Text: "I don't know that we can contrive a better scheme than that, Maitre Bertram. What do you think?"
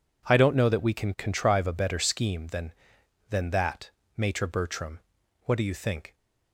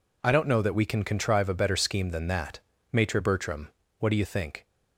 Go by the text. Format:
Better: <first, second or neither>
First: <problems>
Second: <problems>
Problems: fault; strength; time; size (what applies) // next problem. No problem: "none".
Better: second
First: says "than" twice; at 3.2 s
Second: none